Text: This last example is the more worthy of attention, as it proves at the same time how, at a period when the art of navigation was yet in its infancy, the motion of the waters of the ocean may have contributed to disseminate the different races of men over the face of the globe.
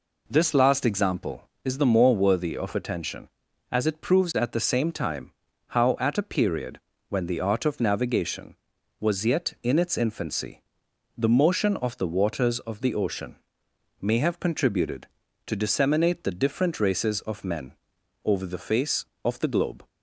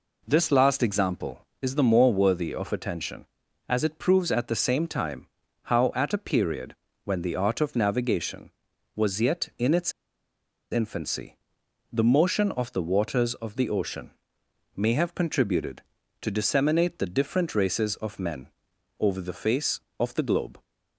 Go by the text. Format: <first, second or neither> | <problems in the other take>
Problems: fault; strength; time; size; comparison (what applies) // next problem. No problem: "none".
first | pauses between "time" and "how"; slight; at 5.2 s; 0.36 s long; slight in the first // pauses between "period" and "when"; slight; at 6.7 s; 0.28 s long; slight in the first // pauses between "its" and "infancy"; noticeable; at 9.9 s; 0.80 s long // pauses between "ocean" and "may"; noticeable; at 14.1 s; 0.66 s long; noticeable in the first // pauses between "men" and "over"; noticeable; at 18.4 s; 0.54 s long; noticeable in the first